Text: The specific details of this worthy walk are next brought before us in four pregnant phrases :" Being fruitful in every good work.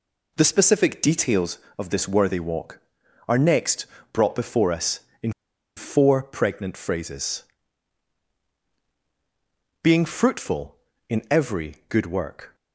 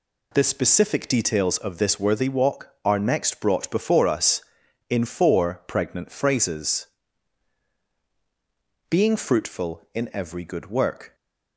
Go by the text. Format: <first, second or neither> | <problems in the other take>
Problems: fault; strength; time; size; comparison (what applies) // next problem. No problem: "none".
second | pauses between "next" and "brought"; slight; at 3.8 s; 0.28 s long // pauses between "in" and "four"; at 5.3 s; 0.45 s long